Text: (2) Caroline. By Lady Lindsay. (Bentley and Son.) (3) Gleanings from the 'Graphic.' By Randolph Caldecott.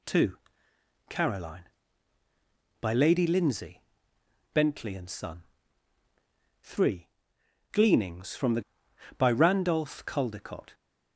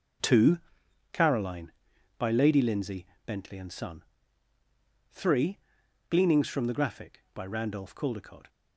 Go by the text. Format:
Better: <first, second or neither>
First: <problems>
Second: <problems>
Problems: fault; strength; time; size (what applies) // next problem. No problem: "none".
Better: second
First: skips "Graphic"; at 8.8 s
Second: none